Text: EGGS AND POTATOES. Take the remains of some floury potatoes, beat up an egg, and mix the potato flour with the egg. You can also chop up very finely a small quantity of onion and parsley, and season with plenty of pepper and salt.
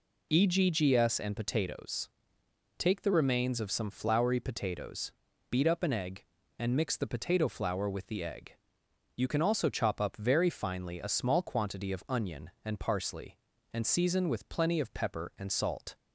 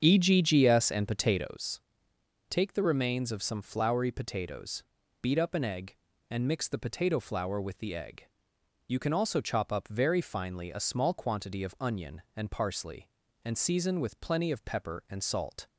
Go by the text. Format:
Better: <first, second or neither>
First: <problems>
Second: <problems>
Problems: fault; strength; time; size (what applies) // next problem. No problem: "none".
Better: first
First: none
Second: starts louder than the rest; strong; until 1.7 s; 7.5 dB